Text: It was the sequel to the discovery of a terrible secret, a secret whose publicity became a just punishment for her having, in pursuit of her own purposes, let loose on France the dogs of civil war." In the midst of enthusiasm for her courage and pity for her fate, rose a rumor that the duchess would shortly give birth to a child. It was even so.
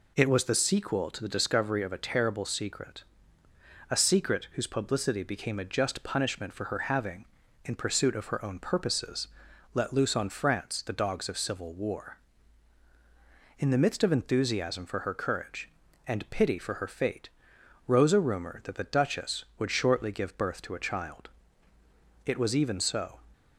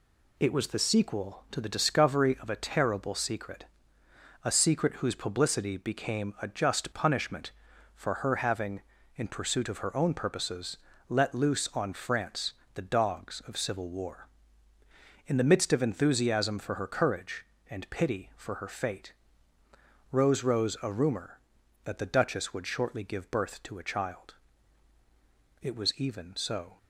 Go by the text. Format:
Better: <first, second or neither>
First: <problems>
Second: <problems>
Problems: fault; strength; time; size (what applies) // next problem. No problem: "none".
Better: first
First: none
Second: pauses between "France" and "the"; slight; at 12.5 s; 0.22 s long // says "rose" twice; at 20.4 s